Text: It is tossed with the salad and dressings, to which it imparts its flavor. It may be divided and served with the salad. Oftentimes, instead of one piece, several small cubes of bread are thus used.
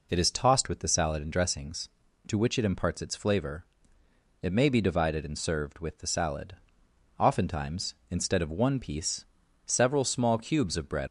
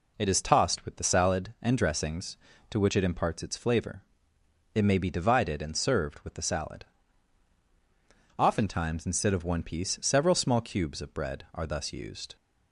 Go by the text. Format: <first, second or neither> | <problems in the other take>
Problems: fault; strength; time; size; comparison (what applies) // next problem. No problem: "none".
second | stops before "are thus used"; at 11.0 s